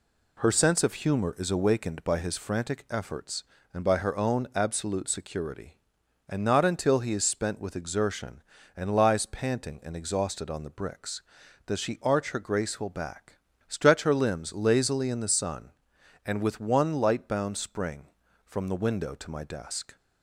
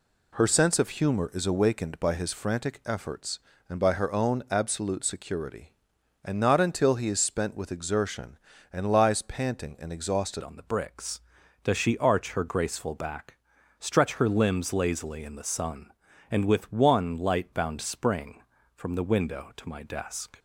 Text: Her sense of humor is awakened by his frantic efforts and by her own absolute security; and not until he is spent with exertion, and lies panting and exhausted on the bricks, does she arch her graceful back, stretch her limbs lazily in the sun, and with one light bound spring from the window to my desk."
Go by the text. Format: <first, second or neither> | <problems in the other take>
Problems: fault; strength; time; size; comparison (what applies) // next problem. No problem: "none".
first | changes voice at "on"; from 10.4 s on; 9.9 s long